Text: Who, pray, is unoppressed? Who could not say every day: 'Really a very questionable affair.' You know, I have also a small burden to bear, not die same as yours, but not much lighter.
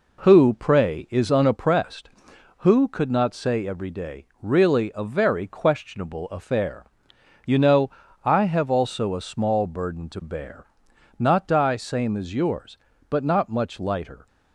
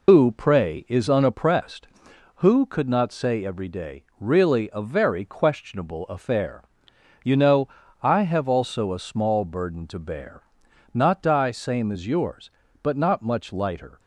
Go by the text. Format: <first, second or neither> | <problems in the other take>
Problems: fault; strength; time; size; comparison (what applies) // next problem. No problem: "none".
first | loses the start of "Who"; at 0.0 s; 120 ms